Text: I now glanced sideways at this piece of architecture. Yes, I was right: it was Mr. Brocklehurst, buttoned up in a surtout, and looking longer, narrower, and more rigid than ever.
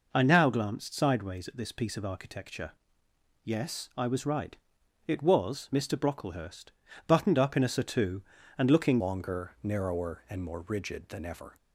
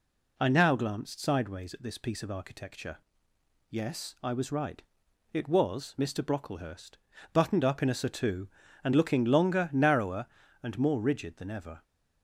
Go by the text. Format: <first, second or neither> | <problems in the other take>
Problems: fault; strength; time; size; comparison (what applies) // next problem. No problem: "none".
second | changes voice at "longer"; from 8.9 s on; 2.6 s long